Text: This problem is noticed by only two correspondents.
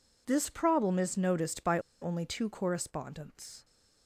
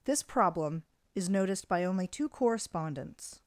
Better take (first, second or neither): second